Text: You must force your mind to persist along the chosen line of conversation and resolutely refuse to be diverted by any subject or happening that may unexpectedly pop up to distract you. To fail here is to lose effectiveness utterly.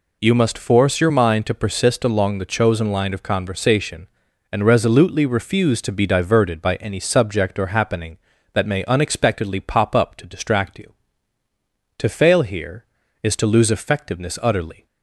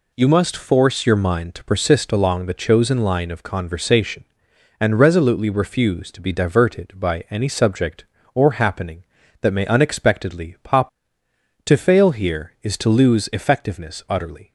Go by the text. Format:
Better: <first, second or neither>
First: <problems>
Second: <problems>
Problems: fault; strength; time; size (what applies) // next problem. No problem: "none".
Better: first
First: none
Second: skips "up to distract you"; at 11.2 s